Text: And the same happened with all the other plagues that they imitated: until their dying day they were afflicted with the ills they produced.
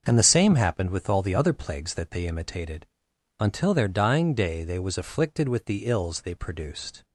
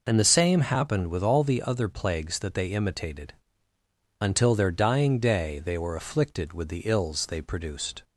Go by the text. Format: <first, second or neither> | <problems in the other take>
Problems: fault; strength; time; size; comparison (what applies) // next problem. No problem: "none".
second | starts louder than the rest; until 1.0 s; 6.5 dB // says "was" for "were"; at 4.7 s